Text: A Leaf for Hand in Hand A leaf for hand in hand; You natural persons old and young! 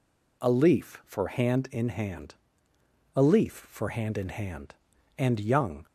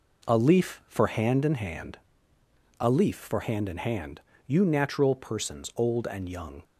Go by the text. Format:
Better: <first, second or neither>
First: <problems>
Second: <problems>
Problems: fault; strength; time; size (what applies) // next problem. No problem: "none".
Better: second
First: pauses between "Hand" and "A"; noticeable; at 2.3 s; 0.80 s long // skips "You natural persons old"; at 4.9 s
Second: pauses between "Hand" and "A"; noticeable; at 1.9 s; 0.82 s long